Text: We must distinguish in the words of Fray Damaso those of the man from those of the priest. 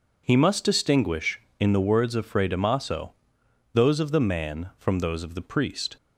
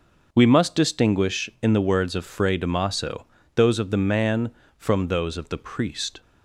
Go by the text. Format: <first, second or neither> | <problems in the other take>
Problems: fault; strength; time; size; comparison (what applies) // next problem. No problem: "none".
second | says "He" for "We"; at 0.2 s // pauses between "Damaso" and "those"; noticeable; at 3.1 s; 0.62 s long; slight in the second